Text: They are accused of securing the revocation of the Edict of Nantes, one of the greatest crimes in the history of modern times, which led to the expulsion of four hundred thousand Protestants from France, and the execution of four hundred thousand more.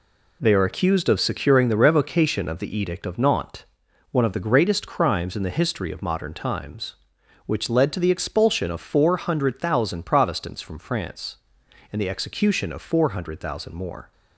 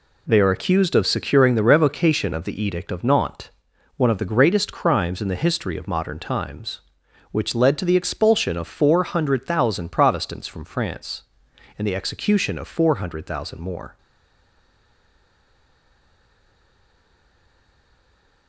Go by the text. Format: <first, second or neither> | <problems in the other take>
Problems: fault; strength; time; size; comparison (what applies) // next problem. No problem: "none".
first | stays silent after the last word; strong; from 13.9 s on; 4.5 s long